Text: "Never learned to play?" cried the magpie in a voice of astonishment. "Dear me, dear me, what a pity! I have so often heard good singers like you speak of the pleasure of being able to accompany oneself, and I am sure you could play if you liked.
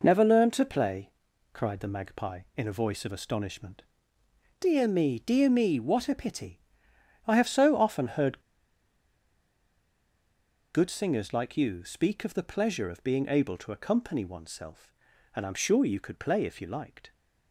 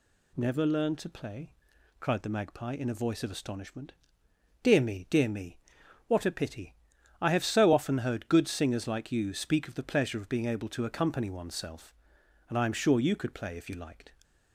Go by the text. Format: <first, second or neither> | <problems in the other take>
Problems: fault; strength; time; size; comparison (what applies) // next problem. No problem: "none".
second | pauses between "heard" and "good"; strong; at 8.3 s; 2.3 s long